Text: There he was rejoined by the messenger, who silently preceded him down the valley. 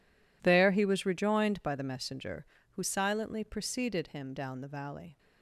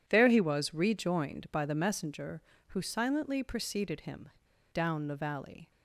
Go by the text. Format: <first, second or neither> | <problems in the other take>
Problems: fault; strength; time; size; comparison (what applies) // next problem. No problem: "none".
first | pauses between "him" and "down"; at 4.2 s; 0.44 s long